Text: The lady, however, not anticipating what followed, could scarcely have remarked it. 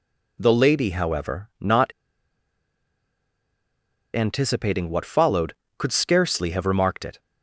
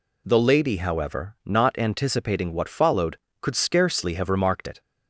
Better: second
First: pauses between "not" and "anticipating"; strong; at 1.9 s; 2.2 s long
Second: none

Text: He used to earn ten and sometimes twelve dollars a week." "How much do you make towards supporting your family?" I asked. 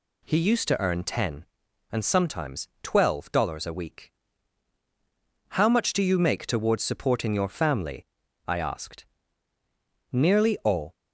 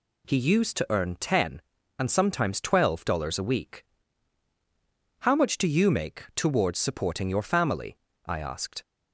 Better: second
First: goes on to say "Nearly all"; noticeable; from 10.1 s on; 0.82 s long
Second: none

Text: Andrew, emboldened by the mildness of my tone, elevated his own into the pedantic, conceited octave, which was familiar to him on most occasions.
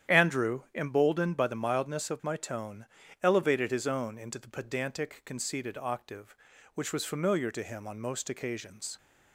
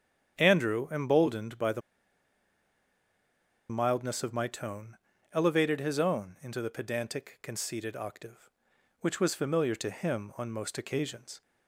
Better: first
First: starts louder than the rest; strong; until 1.2 s; 10 dB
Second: starts louder than the rest; strong; until 1.4 s; 8.5 dB // pauses between "the" and "mildness"; strong; at 1.8 s; 1.8 s long

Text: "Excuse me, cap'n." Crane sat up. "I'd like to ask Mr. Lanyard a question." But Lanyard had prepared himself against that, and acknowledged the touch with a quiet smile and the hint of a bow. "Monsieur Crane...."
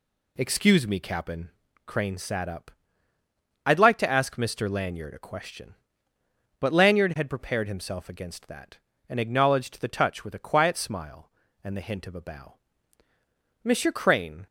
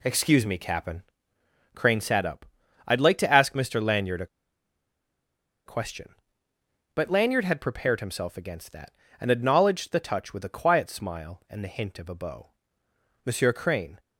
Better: first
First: none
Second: pauses between "a" and "question"; strong; at 4.2 s; 1.4 s long

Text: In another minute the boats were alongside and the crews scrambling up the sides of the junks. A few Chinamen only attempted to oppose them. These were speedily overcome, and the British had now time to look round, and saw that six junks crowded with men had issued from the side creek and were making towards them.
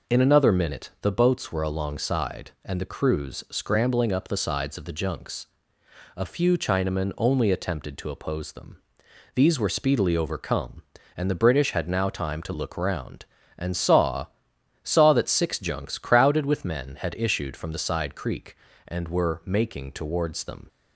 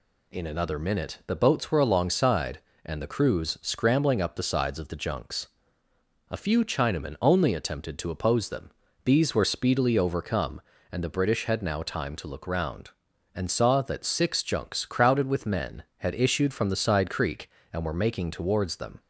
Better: second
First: says "saw" twice; at 14.8 s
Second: none

